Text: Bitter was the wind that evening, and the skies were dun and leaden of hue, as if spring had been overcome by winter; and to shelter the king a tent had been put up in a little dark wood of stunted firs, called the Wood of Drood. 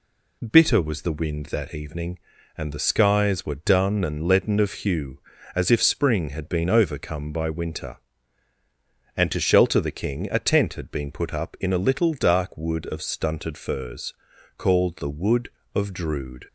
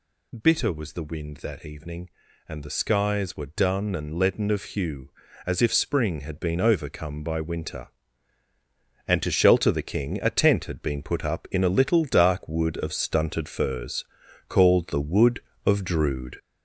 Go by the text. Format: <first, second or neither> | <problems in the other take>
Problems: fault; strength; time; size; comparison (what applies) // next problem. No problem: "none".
first | gets louder; noticeable; throughout; 6 dB